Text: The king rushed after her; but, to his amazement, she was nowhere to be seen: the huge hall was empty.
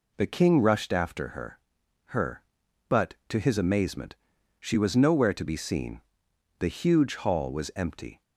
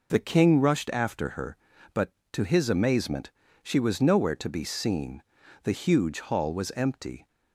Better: second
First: says "her" twice; at 2.0 s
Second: none

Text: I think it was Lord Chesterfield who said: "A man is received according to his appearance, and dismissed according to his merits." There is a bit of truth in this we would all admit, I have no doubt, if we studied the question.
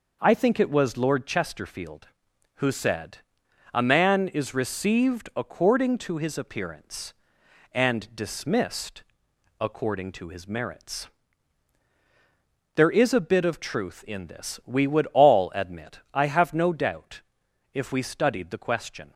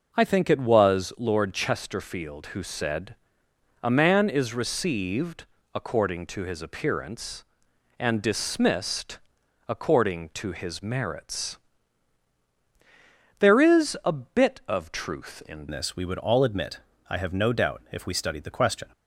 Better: first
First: pauses between "dismissed" and "according"; noticeable; at 9.0 s; 0.58 s long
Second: pauses between "received" and "according"; slight; at 5.4 s; 0.28 s long // pauses between "dismissed" and "according"; noticeable; at 9.1 s; 0.50 s long // changes voice at "this"; from 15.7 s on; 3.1 s long

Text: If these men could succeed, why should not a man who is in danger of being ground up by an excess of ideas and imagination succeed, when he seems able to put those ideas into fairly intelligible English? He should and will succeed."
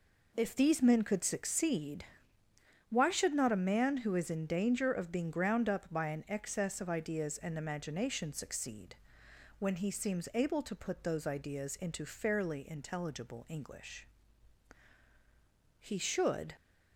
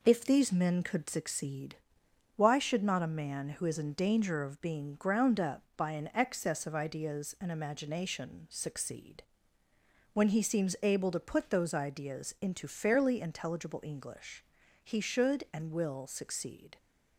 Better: second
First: stops before "and will succeed"; at 16.5 s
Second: none

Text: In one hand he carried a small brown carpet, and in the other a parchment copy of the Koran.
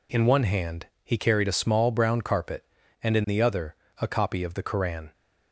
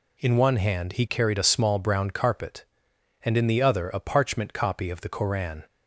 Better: second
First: pauses between "hand" and "he"; slight; at 0.8 s; 0.18 s long // pauses between "other" and "a"; slight; at 3.7 s; 0.24 s long // skips "parchment"; at 4.0 s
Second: none

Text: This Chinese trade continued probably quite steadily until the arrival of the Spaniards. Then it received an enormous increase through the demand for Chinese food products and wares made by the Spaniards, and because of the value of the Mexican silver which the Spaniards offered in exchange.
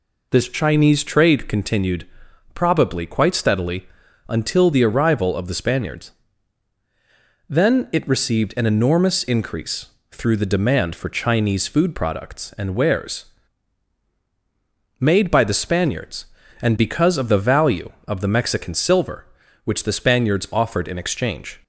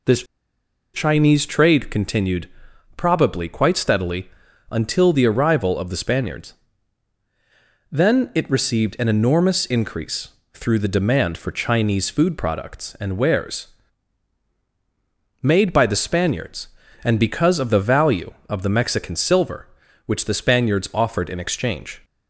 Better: first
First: pauses between "continued" and "probably"; noticeable; at 2.0 s; 0.48 s long // pauses between "steadily" and "until"; at 3.8 s; 0.42 s long // pauses between "increase" and "through"; slight; at 9.8 s; 0.24 s long // pauses between "wares" and "made"; strong; at 13.2 s; 1.7 s long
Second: pauses between "This" and "Chinese"; noticeable; at 0.2 s; 0.70 s long // pauses between "continued" and "probably"; noticeable; at 2.4 s; 0.48 s long // pauses between "steadily" and "until"; at 4.2 s; 0.42 s long // pauses between "increase" and "through"; slight; at 10.2 s; 0.24 s long // pauses between "wares" and "made"; strong; at 13.6 s; 1.7 s long

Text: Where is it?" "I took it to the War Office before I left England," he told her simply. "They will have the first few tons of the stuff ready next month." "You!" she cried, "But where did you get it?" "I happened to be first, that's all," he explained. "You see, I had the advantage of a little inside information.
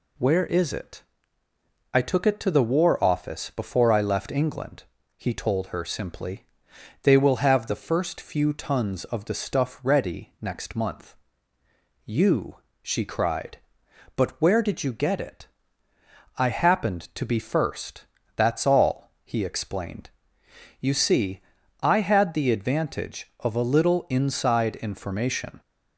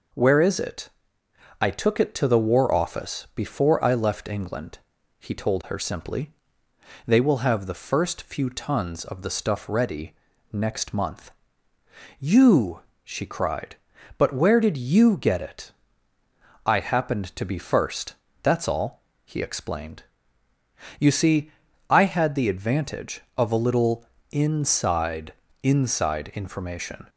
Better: first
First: none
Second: pauses between "ready" and "next"; slight; at 10.1 s; 0.36 s long // pauses between "little" and "inside"; slight; at 24.0 s; 0.26 s long // says "inside" twice; at 25.6 s

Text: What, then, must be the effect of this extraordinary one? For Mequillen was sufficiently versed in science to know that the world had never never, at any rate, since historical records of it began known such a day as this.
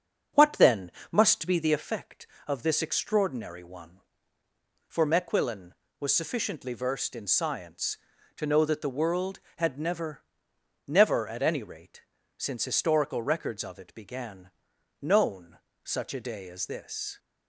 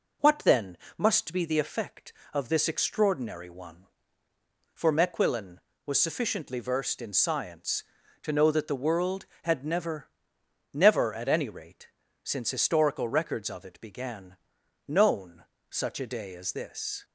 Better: second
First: starts louder than the rest; until 1.8 s; 7 dB // pauses between "never" and "never"; noticeable; at 10.2 s; 0.64 s long // pauses between "began" and "known"; noticeable; at 14.5 s; 0.50 s long // pauses between "known" and "such"; slight; at 15.5 s; 0.26 s long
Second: pauses between "never" and "never"; noticeable; at 10.0 s; 0.64 s long // pauses between "began" and "known"; noticeable; at 14.3 s; 0.50 s long // pauses between "known" and "such"; slight; at 15.4 s; 0.26 s long

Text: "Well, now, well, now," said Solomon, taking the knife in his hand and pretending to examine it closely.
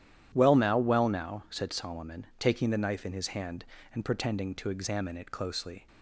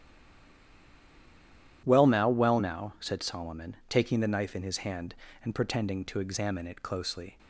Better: first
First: starts louder than the rest; strong; until 1.3 s; 11 dB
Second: stays silent before the first word; noticeable; until 1.8 s; 1.8 s long // starts louder than the rest; strong; until 2.8 s; 11 dB

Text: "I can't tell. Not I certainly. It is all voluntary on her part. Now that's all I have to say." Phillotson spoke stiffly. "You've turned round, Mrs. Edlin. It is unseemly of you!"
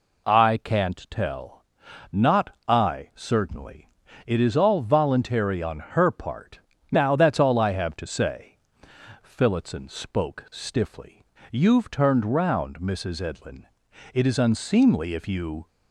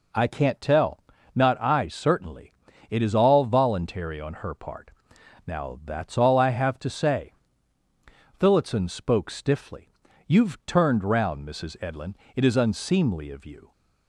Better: second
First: says "if" for "of"; at 15.1 s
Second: none

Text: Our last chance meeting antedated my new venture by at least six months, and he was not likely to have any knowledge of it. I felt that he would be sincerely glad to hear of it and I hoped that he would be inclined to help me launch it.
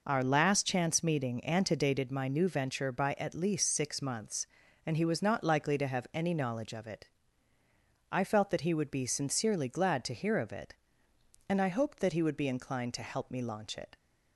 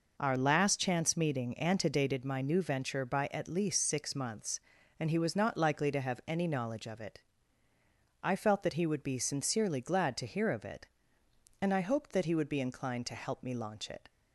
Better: neither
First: none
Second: none

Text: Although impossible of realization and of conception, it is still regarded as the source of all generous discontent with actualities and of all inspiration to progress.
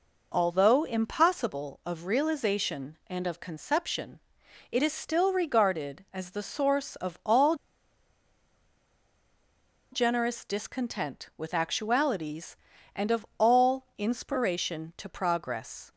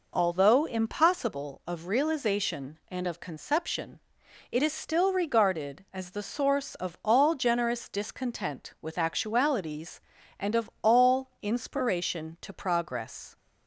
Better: second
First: pauses between "all" and "generous"; strong; at 7.5 s; 2.3 s long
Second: none

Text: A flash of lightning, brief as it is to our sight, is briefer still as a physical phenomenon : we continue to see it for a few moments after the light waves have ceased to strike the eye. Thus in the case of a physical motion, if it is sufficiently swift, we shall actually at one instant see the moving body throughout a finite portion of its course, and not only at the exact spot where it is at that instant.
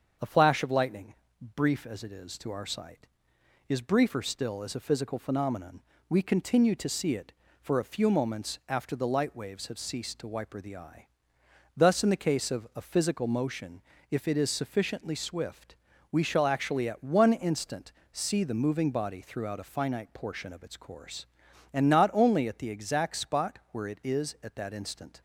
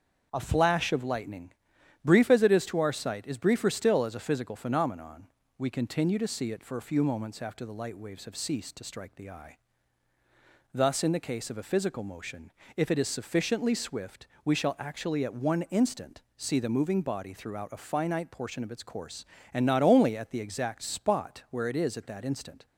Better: second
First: starts louder than the rest; until 1.6 s; 7 dB // says "wiper" for "strike"; at 10.2 s // pauses between "instant" and "see"; slight; at 17.9 s; 0.18 s long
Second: starts louder than the rest; until 1.3 s; 7 dB

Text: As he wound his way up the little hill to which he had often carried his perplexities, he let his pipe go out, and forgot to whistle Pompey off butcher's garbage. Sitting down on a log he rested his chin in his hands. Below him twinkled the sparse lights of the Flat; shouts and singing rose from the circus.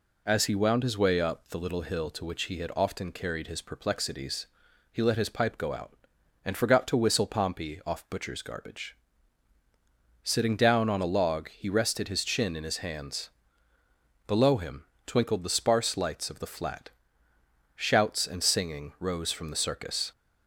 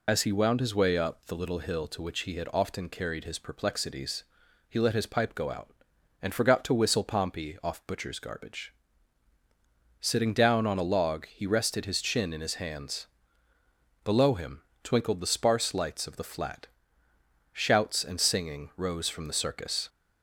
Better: first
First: pauses between "him" and "twinkled"; slight; at 14.8 s; 0.22 s long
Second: loses the start of "As"; at 0.0 s; 55 ms // pauses between "him" and "twinkled"; slight; at 14.6 s; 0.22 s long

